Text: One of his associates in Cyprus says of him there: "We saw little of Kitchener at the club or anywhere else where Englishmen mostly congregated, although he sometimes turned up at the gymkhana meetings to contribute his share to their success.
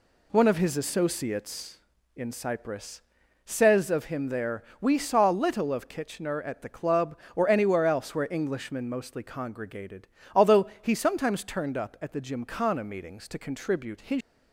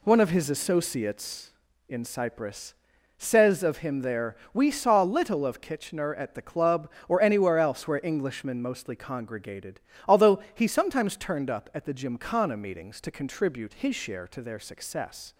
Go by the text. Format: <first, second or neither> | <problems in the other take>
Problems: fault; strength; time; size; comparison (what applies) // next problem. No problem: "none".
second | pauses between "Cyprus" and "says"; at 3.0 s; 0.44 s long; also in the second // stops before "share to their success"; at 14.2 s